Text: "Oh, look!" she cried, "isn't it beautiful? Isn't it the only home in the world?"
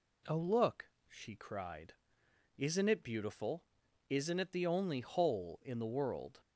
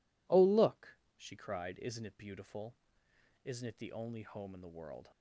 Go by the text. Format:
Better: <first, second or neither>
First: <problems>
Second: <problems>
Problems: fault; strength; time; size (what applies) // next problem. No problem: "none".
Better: second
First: says "hole" for "home"; at 5.0 s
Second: none